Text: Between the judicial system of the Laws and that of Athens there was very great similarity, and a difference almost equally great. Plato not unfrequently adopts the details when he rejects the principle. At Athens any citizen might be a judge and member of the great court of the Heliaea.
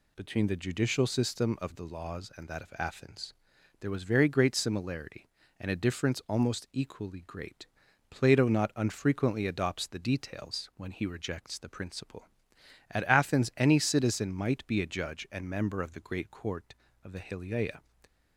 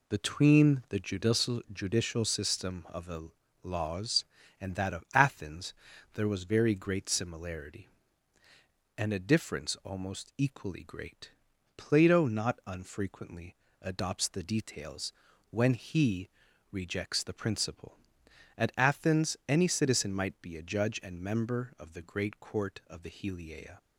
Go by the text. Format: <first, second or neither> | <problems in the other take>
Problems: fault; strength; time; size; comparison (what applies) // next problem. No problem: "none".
first | says "judicial" twice; at 1.7 s // pauses between "the" and "Laws"; slight; at 3.2 s; 0.34 s long // pauses between "Athens" and "there"; at 5.7 s; 0.40 s long; noticeable in the first // pauses between "unfrequently" and "adopts"; slight; at 13.5 s; 0.26 s long // pauses between "details" and "when"; at 15.1 s; 0.38 s long // pauses between "he" and "rejects"; at 16.2 s; 0.40 s long